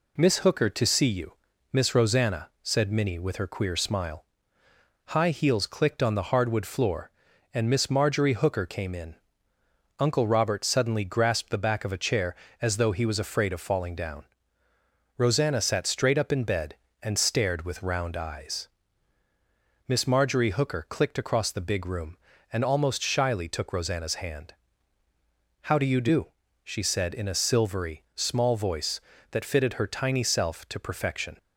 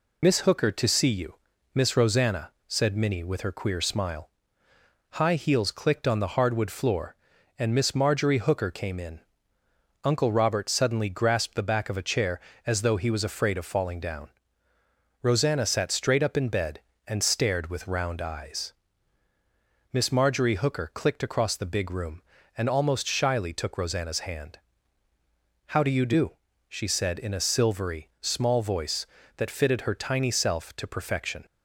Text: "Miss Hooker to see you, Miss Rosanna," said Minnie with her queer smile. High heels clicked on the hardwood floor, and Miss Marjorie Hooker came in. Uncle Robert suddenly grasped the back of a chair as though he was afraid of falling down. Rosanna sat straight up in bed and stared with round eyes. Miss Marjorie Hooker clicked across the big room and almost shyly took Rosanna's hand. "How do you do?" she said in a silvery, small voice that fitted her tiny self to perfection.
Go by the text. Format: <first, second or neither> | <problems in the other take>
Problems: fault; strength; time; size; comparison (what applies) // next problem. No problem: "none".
first | loses the start of "Miss"; at 0.2 s; 35 ms